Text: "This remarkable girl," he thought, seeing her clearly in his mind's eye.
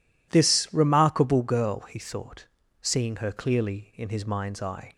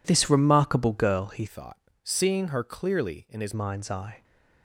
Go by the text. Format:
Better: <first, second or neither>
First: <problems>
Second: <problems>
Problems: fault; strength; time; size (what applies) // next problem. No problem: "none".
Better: first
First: none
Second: changes voice from "thought" to "his"; from 1.4 to 3.5 s; 2.1 s long